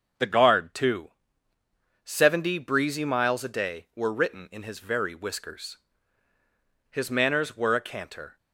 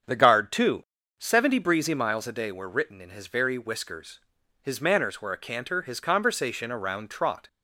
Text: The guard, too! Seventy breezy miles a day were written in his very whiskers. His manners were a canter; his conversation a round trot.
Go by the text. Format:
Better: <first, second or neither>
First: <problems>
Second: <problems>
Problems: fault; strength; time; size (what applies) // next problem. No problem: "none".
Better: second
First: starts louder than the rest; until 2.1 s; 6.5 dB // stops before "his conversation a round trot"; at 8.3 s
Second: starts louder than the rest; strong; until 1.4 s; 7.5 dB